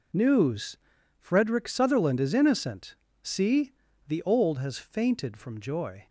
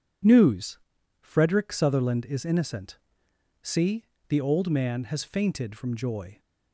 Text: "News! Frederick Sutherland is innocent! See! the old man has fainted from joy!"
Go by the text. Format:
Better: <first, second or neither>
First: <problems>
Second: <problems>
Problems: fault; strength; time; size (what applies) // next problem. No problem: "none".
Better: second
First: skips "man"; at 4.5 s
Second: none